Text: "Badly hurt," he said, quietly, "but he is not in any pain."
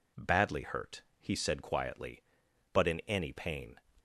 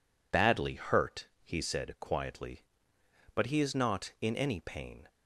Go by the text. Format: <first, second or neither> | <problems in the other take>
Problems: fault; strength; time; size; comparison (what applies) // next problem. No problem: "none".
second | skips "he is not"; at 2.8 s